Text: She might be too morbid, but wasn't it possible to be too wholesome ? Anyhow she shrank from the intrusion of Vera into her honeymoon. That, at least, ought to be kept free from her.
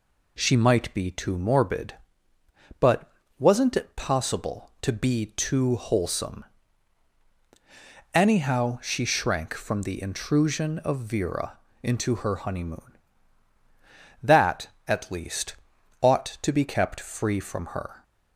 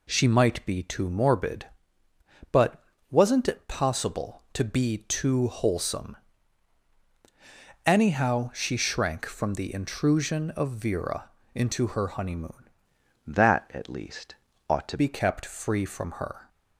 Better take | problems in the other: first | pauses between "but" and "wasn't"; slight; at 2.8 s; 0.28 s long; slight in the first // pauses between "Vera" and "into"; slight; at 11.2 s; 0.26 s long; slight in the first // changes voice from "That" to "to"; from 13.2 to 14.9 s; 1.7 s long

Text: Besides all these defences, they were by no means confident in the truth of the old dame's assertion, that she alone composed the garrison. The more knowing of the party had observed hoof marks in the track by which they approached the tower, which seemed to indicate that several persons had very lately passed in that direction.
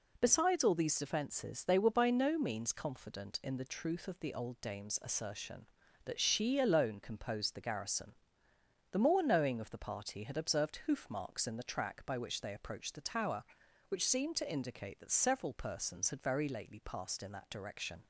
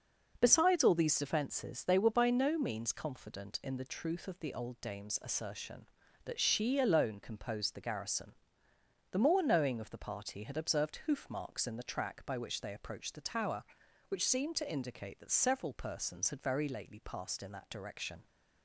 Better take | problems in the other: first | starts louder than the rest; noticeable; until 1.7 s; 5.5 dB

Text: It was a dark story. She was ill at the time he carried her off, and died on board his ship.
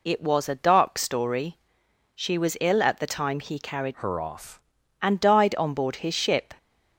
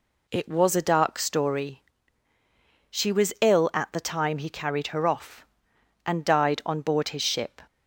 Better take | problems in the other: second | changes voice from "her" to "off"; from 3.9 to 4.6 s; 0.7 s long

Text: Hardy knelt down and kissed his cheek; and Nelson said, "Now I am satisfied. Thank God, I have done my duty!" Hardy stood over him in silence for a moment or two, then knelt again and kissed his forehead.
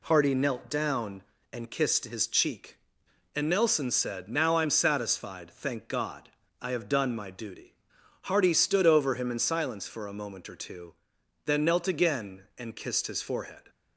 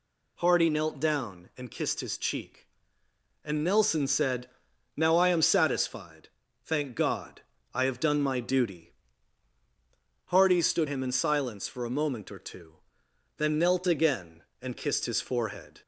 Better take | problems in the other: first | skips "over"; at 10.8 s

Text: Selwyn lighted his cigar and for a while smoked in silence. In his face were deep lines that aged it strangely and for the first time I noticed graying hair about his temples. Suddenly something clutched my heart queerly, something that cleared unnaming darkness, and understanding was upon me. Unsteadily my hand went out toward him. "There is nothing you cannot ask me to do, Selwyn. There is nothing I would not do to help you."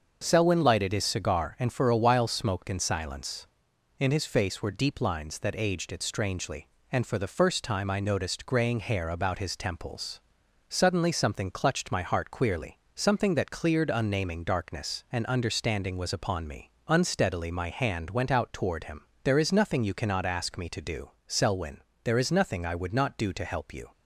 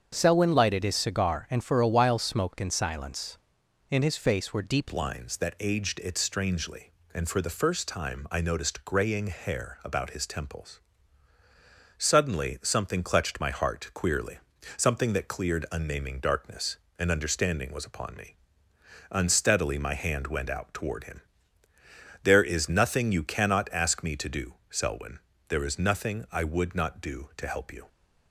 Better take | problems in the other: first | starts louder than the rest; strong; until 1.1 s; 7 dB; also in the first // changes voice at "lines"; from 4.9 s on; 22.9 s long

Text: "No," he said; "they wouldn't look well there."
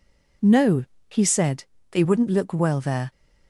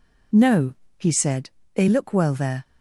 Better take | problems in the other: first | skips "wouldn't"; at 1.8 s

